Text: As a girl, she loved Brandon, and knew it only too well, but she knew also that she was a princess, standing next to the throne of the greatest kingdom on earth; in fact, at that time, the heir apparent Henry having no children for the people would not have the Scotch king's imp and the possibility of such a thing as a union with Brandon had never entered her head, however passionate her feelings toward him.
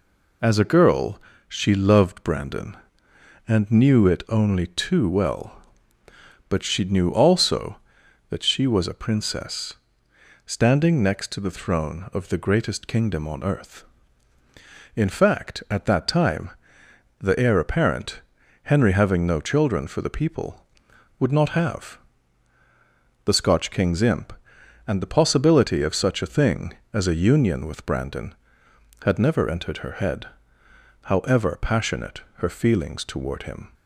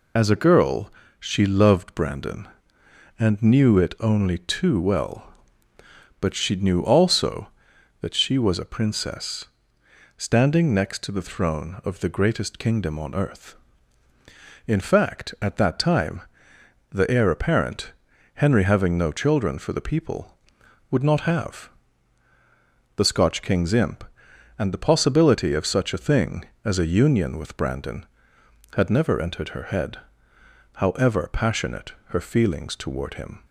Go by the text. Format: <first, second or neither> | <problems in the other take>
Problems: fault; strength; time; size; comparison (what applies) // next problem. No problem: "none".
first | loses the start of "As"; at 0.1 s; 25 ms // pauses between "apparent" and "Henry"; at 17.9 s; 0.40 s long; also in the first // pauses between "have" and "the"; strong; at 21.6 s; 1.2 s long; strong in the first // pauses between "passionate" and "her"; slight; at 31.9 s; 0.16 s long; slight in the first